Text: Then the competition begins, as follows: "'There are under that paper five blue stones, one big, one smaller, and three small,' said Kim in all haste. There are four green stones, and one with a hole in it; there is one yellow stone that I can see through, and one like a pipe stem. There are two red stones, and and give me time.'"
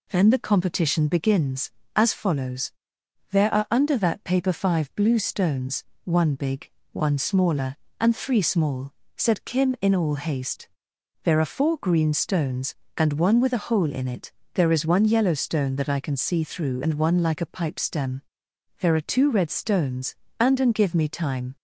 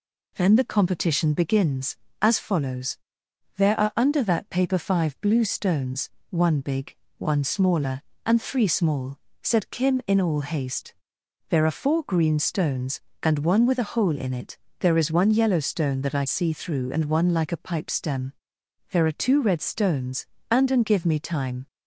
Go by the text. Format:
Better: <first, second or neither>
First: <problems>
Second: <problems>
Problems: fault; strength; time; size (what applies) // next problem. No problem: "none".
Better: first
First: none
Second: skips "can"; at 16.2 s